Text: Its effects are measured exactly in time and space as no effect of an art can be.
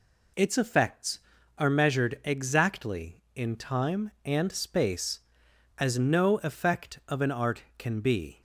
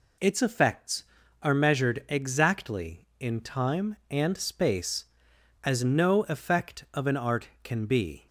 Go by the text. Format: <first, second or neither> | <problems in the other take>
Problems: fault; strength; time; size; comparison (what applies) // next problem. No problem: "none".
neither | none